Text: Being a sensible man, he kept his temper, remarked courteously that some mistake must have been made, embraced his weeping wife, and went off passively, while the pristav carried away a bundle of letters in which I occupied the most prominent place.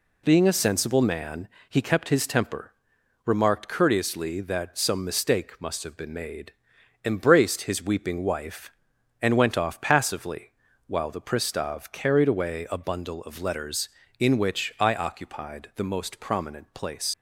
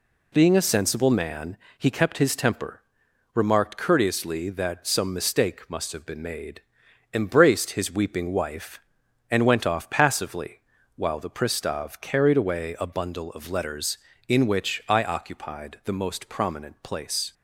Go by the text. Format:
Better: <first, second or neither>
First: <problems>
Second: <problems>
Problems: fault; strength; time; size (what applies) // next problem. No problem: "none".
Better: second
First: leaves "place" unfinished; at 17.1 s; 105 ms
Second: none